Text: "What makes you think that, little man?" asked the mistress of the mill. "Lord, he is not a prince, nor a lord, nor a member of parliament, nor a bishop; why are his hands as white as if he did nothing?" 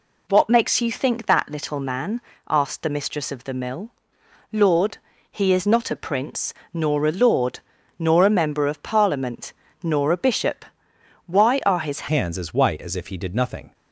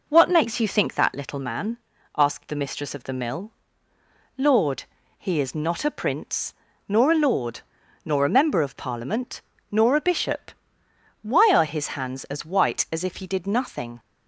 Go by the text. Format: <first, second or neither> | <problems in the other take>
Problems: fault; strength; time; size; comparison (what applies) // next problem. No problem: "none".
second | changes voice at "hands"; from 12.0 s on; 1.7 s long